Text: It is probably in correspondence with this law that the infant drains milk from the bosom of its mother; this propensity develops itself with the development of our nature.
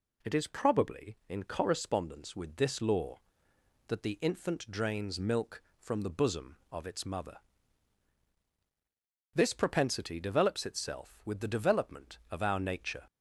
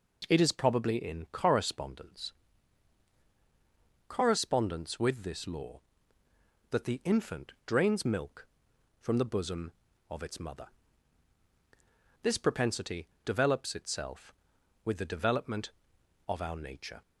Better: first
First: none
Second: says "correspondence" twice; at 4.0 s // pauses between "propensity" and "develops"; slight; at 13.0 s; 0.16 s long

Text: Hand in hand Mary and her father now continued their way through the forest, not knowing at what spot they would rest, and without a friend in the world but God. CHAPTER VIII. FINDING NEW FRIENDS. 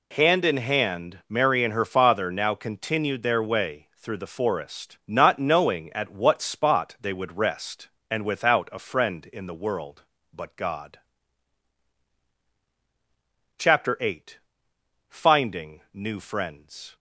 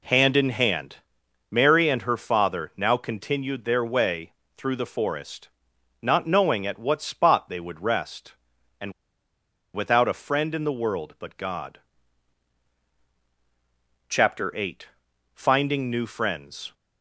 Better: first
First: none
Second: pauses between "hand" and "Mary"; noticeable; at 0.9 s; 0.52 s long // pauses between "way" and "through"; slight; at 4.3 s; 0.24 s long // pauses between "and" and "without"; noticeable; at 8.9 s; 0.82 s long

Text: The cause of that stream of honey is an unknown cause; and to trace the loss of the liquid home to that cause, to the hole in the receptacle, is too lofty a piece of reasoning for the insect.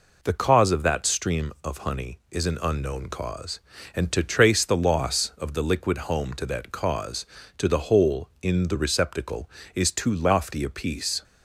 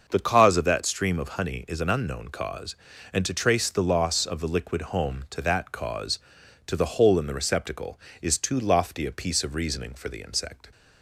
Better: second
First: stops before "of reasoning for the insect"; at 11.2 s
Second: none

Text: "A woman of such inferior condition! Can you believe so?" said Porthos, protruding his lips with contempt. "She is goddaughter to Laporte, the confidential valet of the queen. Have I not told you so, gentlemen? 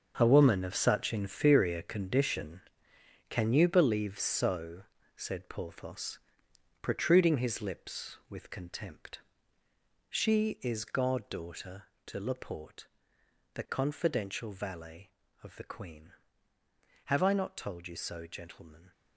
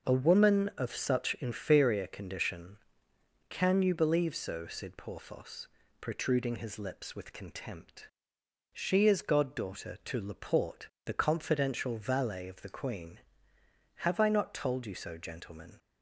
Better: second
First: gets quieter; strong; throughout; 11 dB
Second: none

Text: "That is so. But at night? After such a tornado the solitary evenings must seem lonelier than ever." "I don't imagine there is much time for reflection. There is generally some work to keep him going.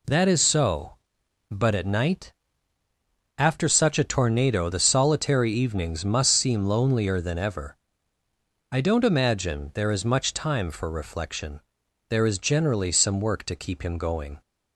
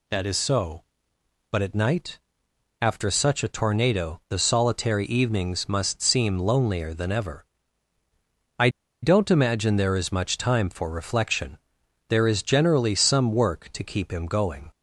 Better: first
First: none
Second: pauses between "I" and "don't"; slight; at 8.6 s; 0.33 s long

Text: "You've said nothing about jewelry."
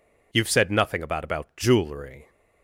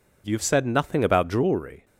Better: second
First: says "about" twice; at 1.2 s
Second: none

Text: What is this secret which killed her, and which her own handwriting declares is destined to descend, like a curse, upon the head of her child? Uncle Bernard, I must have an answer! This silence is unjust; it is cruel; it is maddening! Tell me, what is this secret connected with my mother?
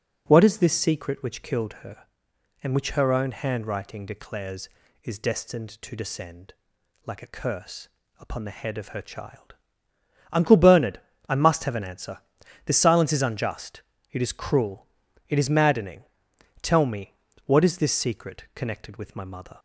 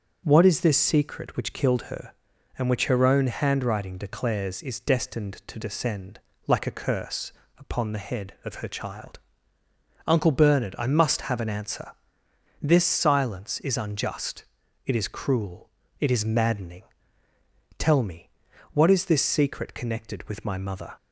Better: neither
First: none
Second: none

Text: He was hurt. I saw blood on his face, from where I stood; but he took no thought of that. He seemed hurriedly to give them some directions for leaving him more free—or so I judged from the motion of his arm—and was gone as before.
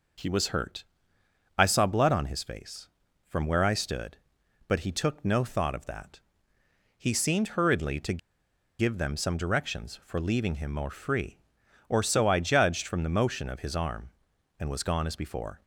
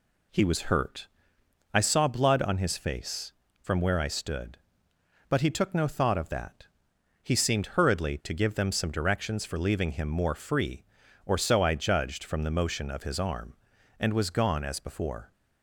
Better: second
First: pauses between "to" and "give"; noticeable; at 8.1 s; 0.60 s long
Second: none

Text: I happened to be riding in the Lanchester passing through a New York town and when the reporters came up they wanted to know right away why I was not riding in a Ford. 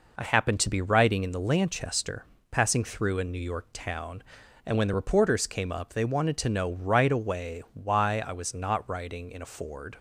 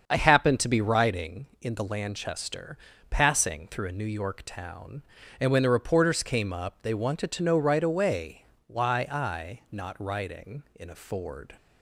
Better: first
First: pauses between "Lanchester" and "passing"; slight; at 2.2 s; 0.23 s long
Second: starts louder than the rest; until 1.0 s; 7 dB // pauses between "Lanchester" and "passing"; slight; at 2.7 s; 0.32 s long // pauses between "away" and "why"; slight; at 8.4 s; 0.22 s long // skips "was"; at 9.6 s

